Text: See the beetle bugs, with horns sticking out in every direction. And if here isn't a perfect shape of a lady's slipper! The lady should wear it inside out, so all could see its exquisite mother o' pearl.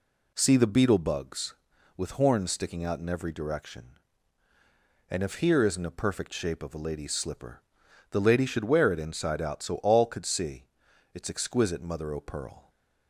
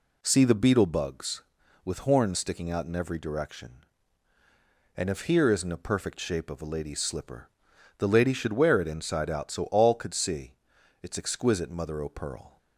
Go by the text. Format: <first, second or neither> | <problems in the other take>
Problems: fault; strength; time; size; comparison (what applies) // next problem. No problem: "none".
neither | pauses between "see" and "its"; noticeable; the same in both